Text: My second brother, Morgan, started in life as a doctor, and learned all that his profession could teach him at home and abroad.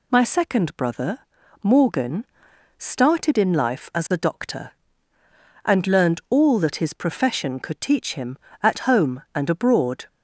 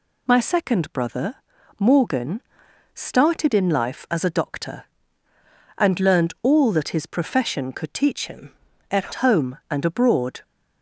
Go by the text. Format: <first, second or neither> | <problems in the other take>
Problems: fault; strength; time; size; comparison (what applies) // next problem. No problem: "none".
first | changes voice from "him" to "at"; from 8.2 to 9.1 s; 0.9 s long